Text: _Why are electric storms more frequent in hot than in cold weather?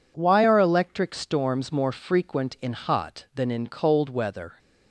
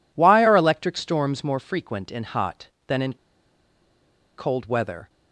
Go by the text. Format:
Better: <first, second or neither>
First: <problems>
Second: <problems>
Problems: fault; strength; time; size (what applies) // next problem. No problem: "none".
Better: first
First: none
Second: pauses between "in" and "cold"; at 3.1 s; 1.2 s long